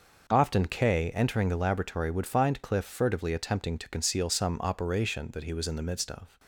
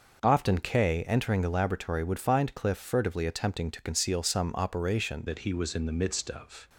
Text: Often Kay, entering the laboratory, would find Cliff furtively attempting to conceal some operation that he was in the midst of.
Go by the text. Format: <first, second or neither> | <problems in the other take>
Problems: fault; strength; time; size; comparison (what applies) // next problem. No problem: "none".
first | changes voice at "that"; from 5.2 s on; 1.4 s long